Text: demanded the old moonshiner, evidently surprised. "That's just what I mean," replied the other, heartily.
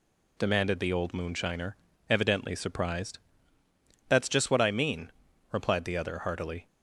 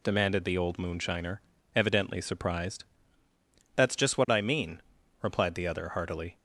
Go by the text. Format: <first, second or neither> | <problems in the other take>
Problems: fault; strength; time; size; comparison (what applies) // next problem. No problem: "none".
neither | none